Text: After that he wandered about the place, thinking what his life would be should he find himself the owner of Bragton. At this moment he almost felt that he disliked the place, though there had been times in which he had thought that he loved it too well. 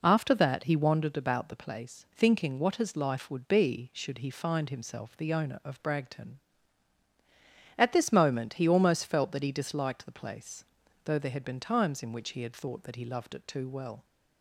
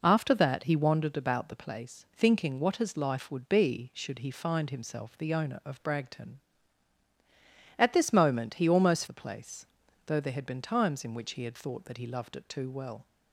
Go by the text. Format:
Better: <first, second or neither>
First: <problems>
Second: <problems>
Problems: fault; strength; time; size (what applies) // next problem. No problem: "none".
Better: first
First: none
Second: skips "felt that he disliked"; at 9.0 s